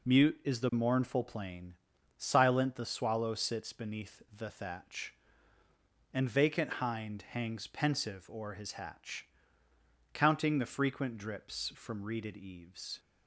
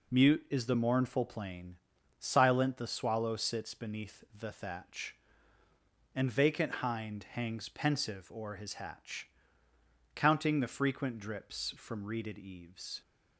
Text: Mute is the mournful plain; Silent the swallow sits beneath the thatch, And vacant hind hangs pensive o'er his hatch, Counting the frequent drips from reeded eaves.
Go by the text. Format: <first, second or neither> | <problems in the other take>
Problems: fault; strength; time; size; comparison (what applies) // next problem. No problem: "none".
neither | none